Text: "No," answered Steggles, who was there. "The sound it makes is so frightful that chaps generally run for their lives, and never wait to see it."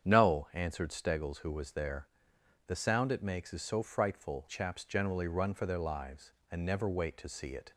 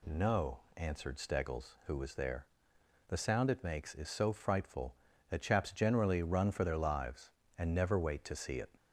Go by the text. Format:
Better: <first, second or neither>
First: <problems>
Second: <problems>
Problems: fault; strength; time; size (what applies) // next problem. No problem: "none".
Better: second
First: starts louder than the rest; strong; until 1.1 s; 8.5 dB // skips "that"; at 4.4 s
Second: none